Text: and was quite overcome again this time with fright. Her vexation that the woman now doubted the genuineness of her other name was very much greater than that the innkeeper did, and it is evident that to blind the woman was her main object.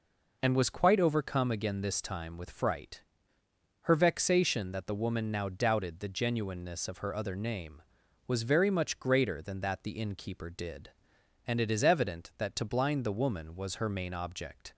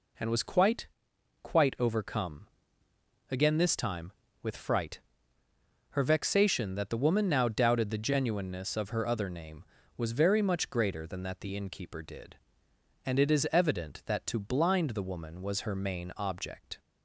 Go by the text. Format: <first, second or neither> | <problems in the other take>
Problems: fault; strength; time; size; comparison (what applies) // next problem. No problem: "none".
first | says "quite" twice; at 1.4 s // pauses between "overcome" and "again"; noticeable; at 2.4 s; 0.82 s long